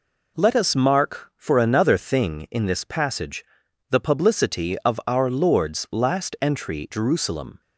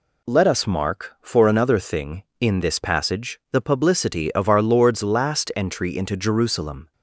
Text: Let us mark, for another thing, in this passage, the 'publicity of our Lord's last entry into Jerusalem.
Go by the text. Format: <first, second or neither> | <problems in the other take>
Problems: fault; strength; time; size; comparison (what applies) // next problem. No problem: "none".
second | skips "into"; at 6.9 s